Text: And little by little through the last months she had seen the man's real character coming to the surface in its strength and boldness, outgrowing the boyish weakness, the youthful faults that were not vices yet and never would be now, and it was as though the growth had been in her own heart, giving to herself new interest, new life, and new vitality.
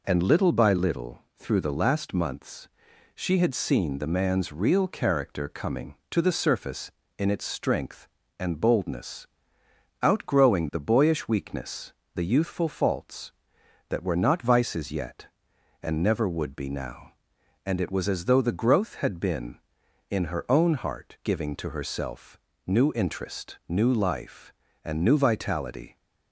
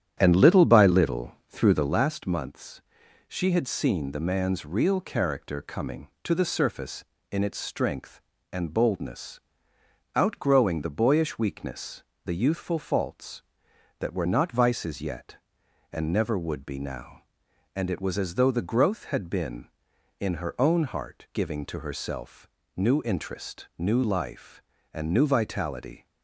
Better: first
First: pauses between "months" and "she"; noticeable; at 2.6 s; 0.48 s long // pauses between "herself" and "new"; slight; at 22.3 s; 0.28 s long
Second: starts louder than the rest; strong; until 2.1 s; 9.5 dB // pauses between "months" and "she"; noticeable; at 2.8 s; 0.48 s long // pauses between "herself" and "new"; slight; at 22.4 s; 0.28 s long

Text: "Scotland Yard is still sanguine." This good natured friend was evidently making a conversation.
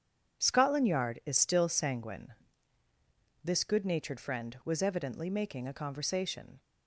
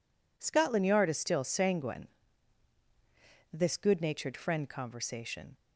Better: first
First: none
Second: skips "was evidently making a"; at 4.6 s

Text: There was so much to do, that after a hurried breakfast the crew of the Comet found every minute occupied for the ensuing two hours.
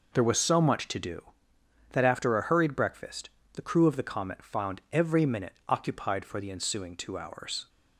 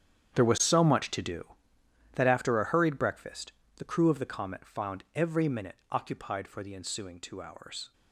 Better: first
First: pauses between "breakfast" and "the"; slight; at 3.2 s; 0.24 s long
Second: gets quieter; strong; throughout; 16.5 dB // pauses between "breakfast" and "the"; slight; at 3.5 s; 0.24 s long

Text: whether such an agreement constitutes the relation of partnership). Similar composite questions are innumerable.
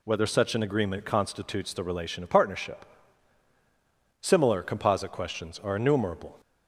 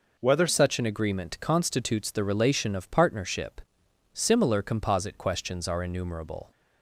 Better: first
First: none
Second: changes voice at "such"; from 0.4 s on; 6.1 s long

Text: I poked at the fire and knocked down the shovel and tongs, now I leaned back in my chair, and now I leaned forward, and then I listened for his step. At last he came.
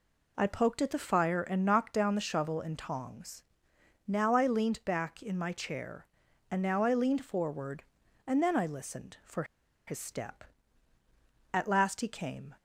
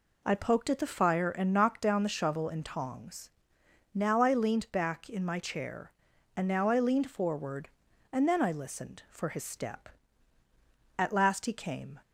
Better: second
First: pauses between "for" and "his"; at 9.4 s; 0.43 s long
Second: none

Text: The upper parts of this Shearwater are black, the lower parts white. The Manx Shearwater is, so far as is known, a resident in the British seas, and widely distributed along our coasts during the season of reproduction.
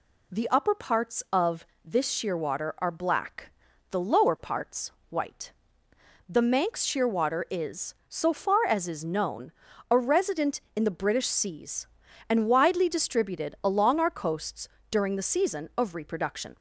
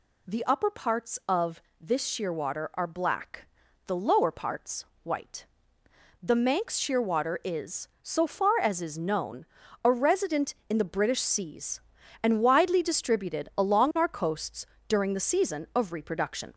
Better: first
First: pauses between "of" and "this"; slight; at 1.6 s; 0.18 s long // pauses between "parts" and "white"; slight; at 4.9 s; 0.20 s long // pauses between "coasts" and "during"; slight; at 14.6 s; 0.22 s long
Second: gets louder; slight; throughout; 2.5 dB // pauses between "of" and "this"; slight; at 1.6 s; 0.18 s long // pauses between "parts" and "white"; slight; at 4.8 s; 0.20 s long // pauses between "coasts" and "during"; slight; at 14.6 s; 0.22 s long

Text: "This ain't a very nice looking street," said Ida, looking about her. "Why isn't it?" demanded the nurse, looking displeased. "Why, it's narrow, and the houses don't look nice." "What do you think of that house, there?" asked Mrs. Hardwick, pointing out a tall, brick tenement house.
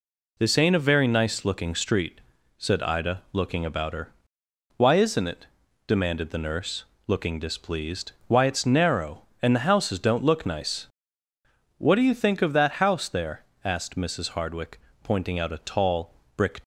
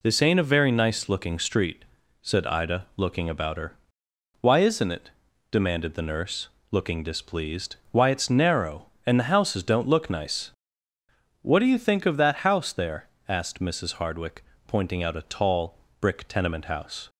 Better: second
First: stops before "tenement house"; at 16.6 s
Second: none

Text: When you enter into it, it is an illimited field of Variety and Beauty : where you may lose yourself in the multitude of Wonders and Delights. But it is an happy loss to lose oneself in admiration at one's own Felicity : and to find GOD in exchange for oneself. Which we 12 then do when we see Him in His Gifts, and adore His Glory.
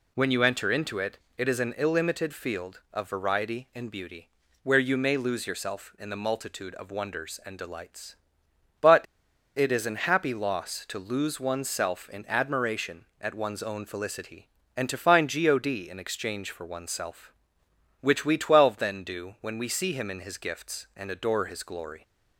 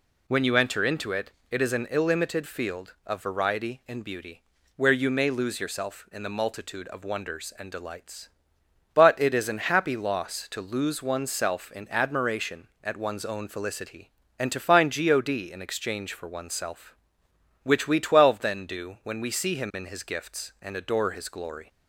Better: second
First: pauses between "But" and "it"; noticeable; at 9.0 s; 0.52 s long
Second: none

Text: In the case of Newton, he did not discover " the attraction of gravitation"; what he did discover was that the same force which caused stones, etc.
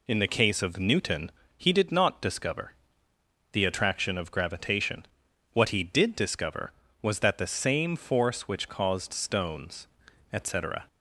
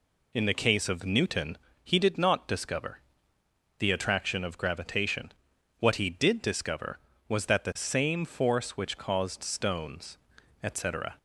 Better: neither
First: none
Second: none

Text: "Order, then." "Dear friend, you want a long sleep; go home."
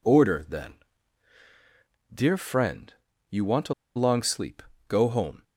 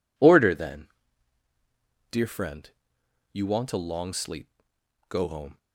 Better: second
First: pauses between "a" and "long"; slight; at 3.7 s; 0.22 s long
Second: none

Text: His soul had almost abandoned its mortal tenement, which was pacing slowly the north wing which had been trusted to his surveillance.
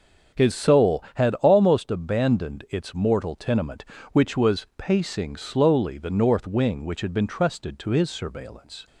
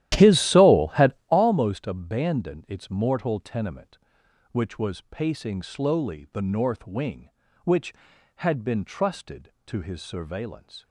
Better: first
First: none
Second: starts louder than the rest; strong; until 1.5 s; 13 dB // pauses between "had" and "almost"; slight; at 1.1 s; 0.16 s long

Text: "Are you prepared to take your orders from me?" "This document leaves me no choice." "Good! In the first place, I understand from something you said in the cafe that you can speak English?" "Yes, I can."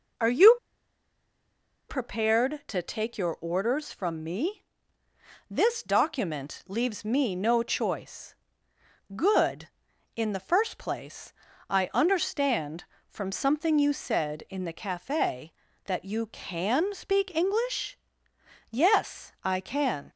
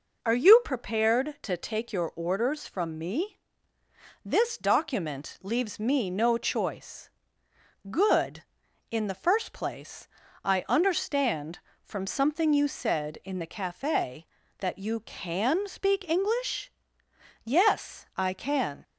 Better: second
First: pauses between "you" and "prepared"; strong; at 0.5 s; 1.3 s long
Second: none

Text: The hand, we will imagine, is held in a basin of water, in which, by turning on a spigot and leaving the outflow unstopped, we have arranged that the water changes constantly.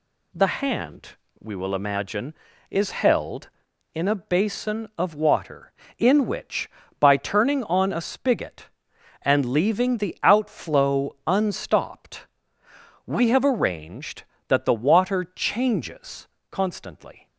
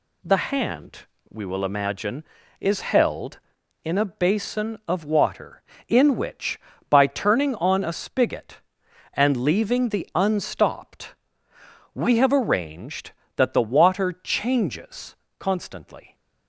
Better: first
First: pauses between "changes" and "constantly"; slight; at 16.2 s; 0.24 s long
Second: skips "outflow"; at 10.1 s // pauses between "changes" and "constantly"; slight; at 15.1 s; 0.24 s long

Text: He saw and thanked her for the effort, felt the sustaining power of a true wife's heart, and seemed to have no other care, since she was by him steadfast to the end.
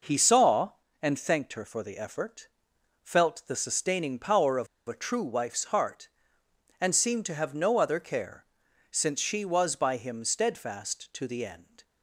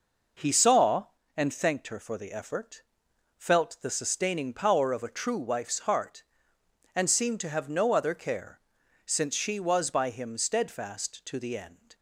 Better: second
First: pauses between "of" and "a"; slight; at 4.6 s; 0.20 s long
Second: none

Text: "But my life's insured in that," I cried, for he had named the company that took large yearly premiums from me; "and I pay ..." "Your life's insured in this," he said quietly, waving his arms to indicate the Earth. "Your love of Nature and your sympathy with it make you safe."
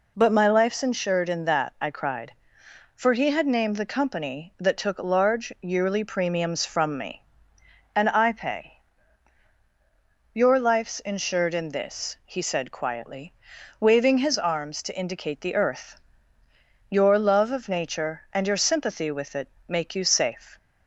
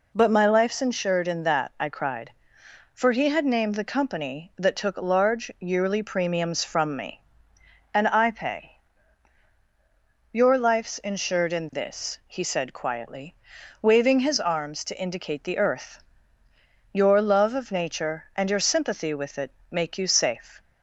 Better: neither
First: pauses between "it" and "make"; slight; at 19.4 s; 0.20 s long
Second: pauses between "it" and "make"; slight; at 19.4 s; 0.20 s long

